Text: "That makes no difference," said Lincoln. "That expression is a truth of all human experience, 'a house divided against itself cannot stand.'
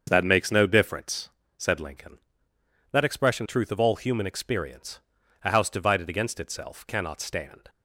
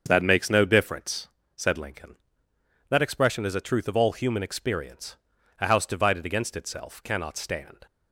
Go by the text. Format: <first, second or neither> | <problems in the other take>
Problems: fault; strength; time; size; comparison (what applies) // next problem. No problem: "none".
second | starts louder than the rest; until 1.0 s; 6.5 dB; also in the second // skips "is a"; at 3.4 s